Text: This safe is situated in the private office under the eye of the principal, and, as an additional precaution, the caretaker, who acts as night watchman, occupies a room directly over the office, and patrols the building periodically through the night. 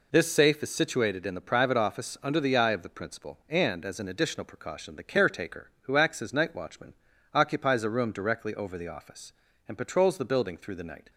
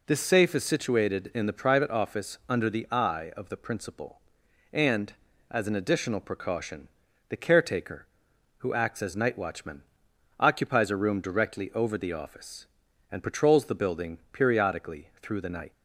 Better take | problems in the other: second | skips "periodically"; at 10.5 s

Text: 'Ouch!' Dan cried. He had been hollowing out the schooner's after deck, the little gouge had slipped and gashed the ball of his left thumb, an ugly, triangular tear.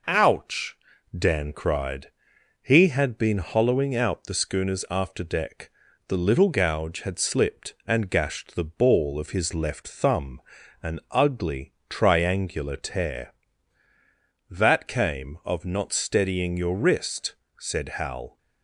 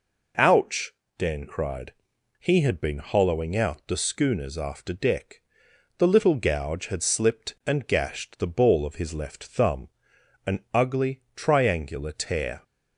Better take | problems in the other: second | goes on to say "That came of not steadying your wrist said Hal"; strong; from 14.4 s on; 3.9 s long

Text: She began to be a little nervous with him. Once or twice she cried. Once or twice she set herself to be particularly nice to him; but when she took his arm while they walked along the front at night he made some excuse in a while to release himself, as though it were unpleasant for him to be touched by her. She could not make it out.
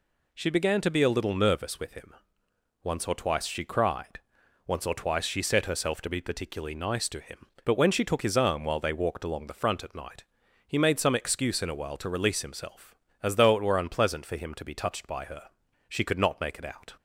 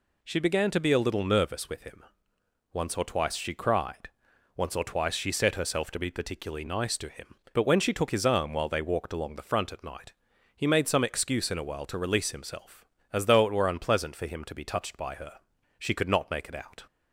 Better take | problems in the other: neither | pauses between "night" and "he"; the same in both

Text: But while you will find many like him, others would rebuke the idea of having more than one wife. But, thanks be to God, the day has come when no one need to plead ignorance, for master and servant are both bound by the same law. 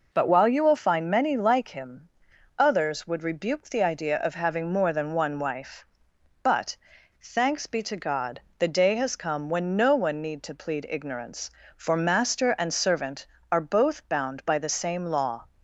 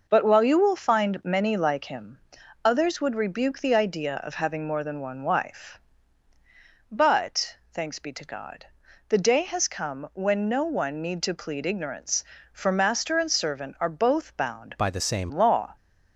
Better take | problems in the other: first | changes voice from "by" to "same"; from 14.7 to 15.3 s; 0.6 s long

